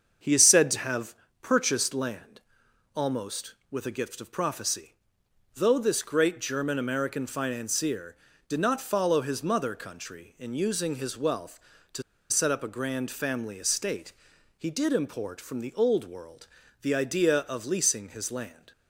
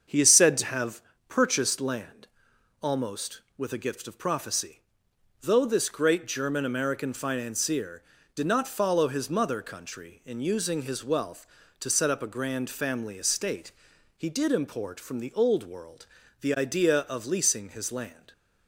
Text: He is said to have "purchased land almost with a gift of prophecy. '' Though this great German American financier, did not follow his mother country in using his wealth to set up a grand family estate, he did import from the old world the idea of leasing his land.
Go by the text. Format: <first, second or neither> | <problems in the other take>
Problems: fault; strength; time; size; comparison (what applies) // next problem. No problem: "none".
second | starts louder than the rest; until 1.4 s; 7 dB; also in the second // pauses between "have" and "purchased"; slight; at 1.1 s; 0.26 s long; slight in the second // pauses between "land" and "almost"; noticeable; at 2.3 s; 0.54 s long; noticeable in the second // pauses between "to" and "set"; slight; at 12.0 s; 0.29 s long // pauses between "world" and "the"; slight; at 16.4 s; 0.34 s long; slight in the second